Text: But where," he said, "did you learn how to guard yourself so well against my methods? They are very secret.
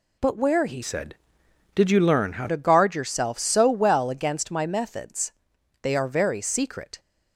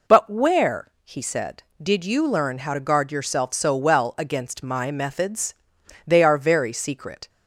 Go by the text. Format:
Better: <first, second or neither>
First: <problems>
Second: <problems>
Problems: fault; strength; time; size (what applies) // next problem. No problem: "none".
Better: second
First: changes voice from "said" to "how"; from 0.8 to 2.4 s; 1.6 s long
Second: none